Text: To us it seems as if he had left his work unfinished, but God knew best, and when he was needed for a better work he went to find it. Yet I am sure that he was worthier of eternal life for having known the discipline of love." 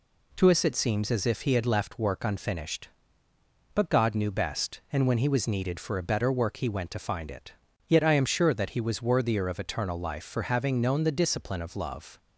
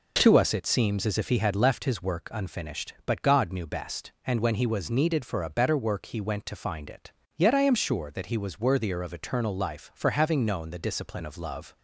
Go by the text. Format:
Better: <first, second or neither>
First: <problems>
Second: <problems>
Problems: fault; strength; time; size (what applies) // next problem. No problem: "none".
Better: second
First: skips "his"; at 1.9 s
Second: none